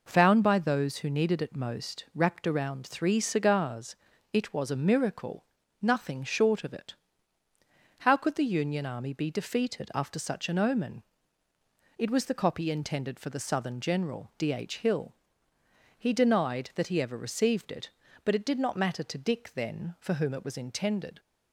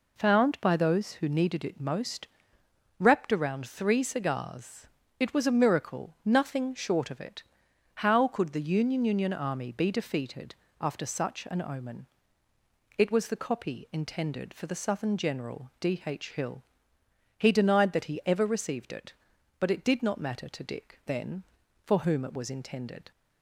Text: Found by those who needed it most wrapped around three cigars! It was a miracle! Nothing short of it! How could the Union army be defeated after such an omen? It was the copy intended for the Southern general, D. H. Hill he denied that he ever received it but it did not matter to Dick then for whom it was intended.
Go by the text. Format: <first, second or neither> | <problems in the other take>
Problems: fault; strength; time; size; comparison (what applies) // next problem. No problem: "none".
first | pauses between "most" and "wrapped"; noticeable; at 2.2 s; 0.72 s long // says "Union" twice; at 9.0 s // pauses between "defeated" and "after"; slight; at 10.5 s; 0.26 s long // pauses between "Hill" and "he"; noticeable; at 16.6 s; 0.76 s long; noticeable in the first